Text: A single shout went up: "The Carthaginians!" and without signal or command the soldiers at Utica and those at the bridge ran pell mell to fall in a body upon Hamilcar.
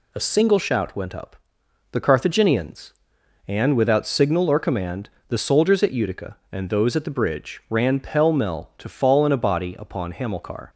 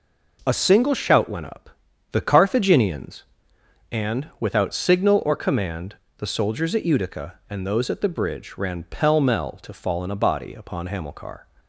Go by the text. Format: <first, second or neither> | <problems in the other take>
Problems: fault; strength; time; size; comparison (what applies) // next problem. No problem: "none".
neither | pauses between "command" and "the"; slight; the same in both